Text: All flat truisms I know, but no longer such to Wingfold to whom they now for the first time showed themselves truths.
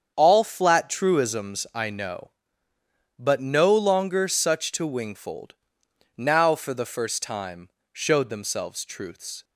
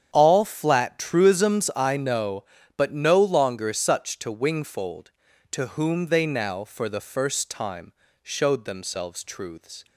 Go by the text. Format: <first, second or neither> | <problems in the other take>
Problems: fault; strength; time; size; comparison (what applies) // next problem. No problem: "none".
second | starts louder than the rest; strong; until 1.1 s; 7.5 dB; strong in the second // skips "to whom they"; at 5.8 s // pauses between "time" and "showed"; slight; at 7.6 s; 0.22 s long; slight in the second